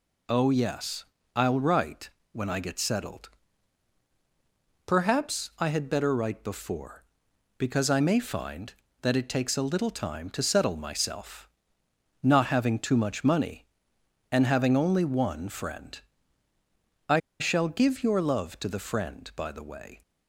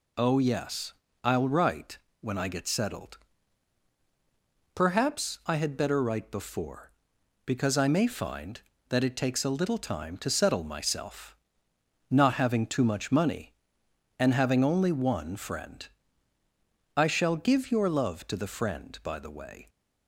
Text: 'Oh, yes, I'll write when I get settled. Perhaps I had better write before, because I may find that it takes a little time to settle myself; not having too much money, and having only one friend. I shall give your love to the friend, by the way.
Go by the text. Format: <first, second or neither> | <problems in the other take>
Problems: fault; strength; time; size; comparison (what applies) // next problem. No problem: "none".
second | pauses between "write" and "when"; slight; at 2.0 s; 0.22 s long; slight in the second // pauses between "I" and "shall"; slight; at 17.1 s; 0.20 s long